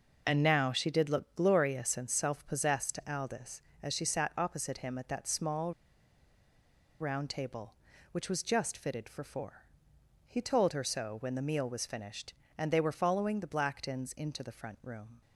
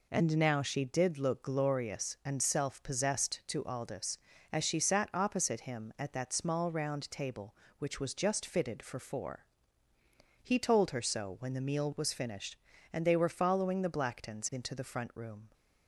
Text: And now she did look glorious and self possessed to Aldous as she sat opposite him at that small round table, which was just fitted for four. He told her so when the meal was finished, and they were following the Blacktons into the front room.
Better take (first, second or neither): second